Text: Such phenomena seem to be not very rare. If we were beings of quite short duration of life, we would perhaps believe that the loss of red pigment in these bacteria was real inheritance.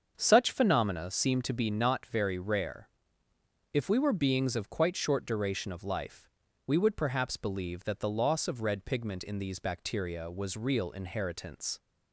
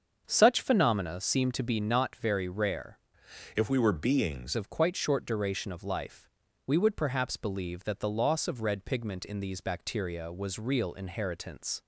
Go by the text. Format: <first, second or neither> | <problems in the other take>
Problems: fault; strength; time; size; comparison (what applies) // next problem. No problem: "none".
first | starts louder than the rest; until 1.2 s; 6.5 dB; also in the first // changes voice from "If" to "beings"; from 3.5 to 4.5 s; 1.0 s long